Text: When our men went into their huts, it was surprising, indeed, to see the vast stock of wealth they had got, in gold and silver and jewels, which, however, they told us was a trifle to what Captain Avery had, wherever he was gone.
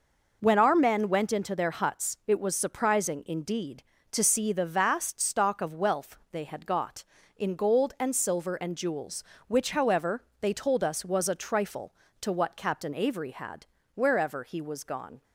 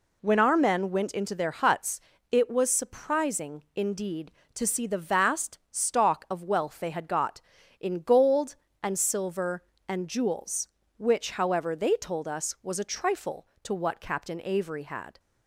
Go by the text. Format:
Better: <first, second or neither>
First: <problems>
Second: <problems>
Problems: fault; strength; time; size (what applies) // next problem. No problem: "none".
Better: first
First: none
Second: stops before "wherever he was gone"; at 15.1 s